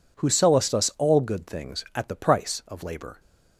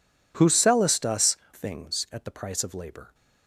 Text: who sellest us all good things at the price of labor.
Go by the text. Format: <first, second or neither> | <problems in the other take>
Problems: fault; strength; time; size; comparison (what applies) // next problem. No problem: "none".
first | skips "all good"; at 1.4 s